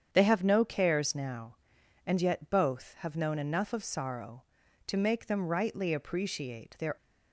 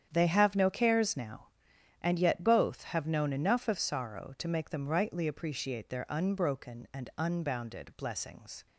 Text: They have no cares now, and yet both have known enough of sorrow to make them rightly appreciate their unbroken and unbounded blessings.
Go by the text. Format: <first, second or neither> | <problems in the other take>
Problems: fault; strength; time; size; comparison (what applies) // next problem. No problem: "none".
second | starts louder than the rest; strong; until 1.1 s; 8 dB; strong in the second // stops before "unbroken and unbounded blessings"; at 6.9 s